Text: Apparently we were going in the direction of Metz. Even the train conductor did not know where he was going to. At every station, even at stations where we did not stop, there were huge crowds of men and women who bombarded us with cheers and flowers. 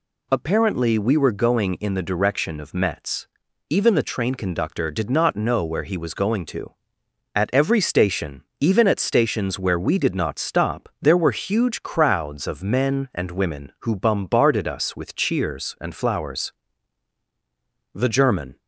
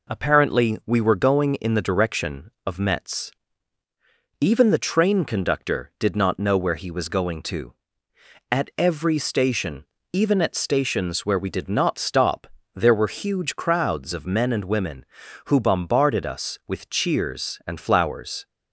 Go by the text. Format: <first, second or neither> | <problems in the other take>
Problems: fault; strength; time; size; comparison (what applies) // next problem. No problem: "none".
second | goes on to say "The German"; noticeable; from 17.9 s on; 0.64 s long